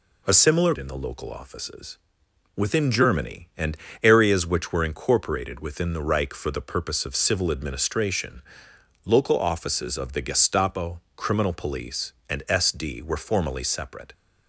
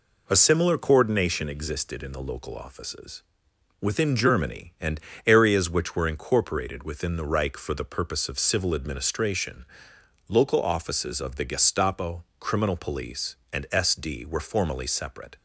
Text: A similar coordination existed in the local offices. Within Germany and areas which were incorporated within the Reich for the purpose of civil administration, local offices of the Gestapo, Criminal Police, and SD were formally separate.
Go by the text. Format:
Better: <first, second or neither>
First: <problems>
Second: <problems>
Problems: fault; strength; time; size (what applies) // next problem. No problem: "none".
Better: second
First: skips "coordination existed"; at 0.7 s // pauses between "and" and "areas"; slight; at 3.7 s; 0.28 s long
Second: pauses between "and" and "areas"; slight; at 4.9 s; 0.28 s long